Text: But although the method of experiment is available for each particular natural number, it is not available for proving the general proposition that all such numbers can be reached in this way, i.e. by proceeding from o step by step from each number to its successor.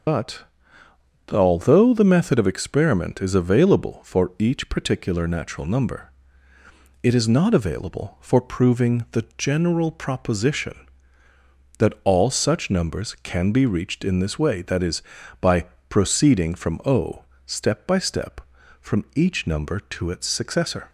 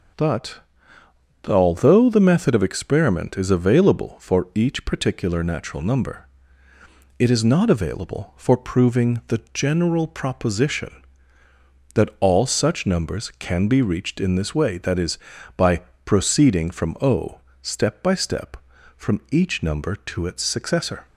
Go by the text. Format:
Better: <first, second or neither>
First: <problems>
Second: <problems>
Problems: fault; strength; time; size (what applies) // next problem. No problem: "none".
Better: second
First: loses the start of "But"; at 0.0 s; 75 ms // starts louder than the rest; until 1.9 s; 6.5 dB // pauses between "But" and "although"; noticeable; at 0.4 s; 0.88 s long // pauses between "by" and "proceeding"; slight; at 15.6 s; 0.24 s long // pauses between "o" and "step"; slight; at 17.2 s; 0.24 s long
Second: starts louder than the rest; until 2.0 s; 6.5 dB // pauses between "But" and "although"; noticeable; at 0.5 s; 0.88 s long // pauses between "by" and "proceeding"; slight; at 15.8 s; 0.24 s long // pauses between "o" and "step"; slight; at 17.3 s; 0.24 s long